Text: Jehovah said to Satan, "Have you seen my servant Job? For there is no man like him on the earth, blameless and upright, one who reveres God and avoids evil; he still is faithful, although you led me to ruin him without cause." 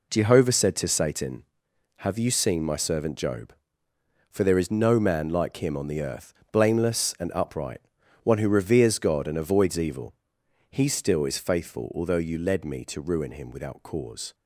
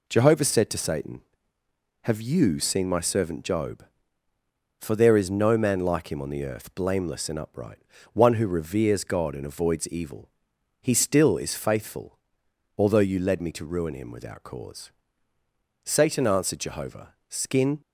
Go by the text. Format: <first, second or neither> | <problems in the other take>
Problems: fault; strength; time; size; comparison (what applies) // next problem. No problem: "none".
first | goes on to say "Satan answered Jehovah Skin"; strong; from 15.8 s on; 1.9 s long